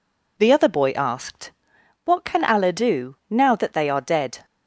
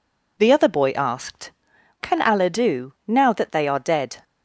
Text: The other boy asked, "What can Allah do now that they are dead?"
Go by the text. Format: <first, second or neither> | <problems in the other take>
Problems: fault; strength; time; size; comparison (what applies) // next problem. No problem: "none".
first | skips "What"; at 1.7 s